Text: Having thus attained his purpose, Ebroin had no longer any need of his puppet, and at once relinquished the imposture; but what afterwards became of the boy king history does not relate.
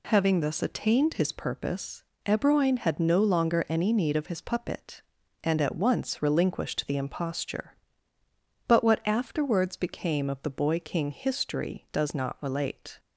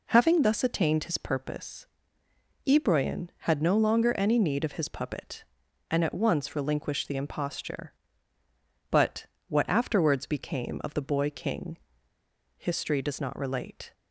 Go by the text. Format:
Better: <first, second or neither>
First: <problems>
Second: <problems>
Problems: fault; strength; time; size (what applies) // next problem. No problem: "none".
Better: first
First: none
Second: pauses between "but" and "what"; slight; at 9.2 s; 0.22 s long // pauses between "king" and "history"; noticeable; at 11.7 s; 0.79 s long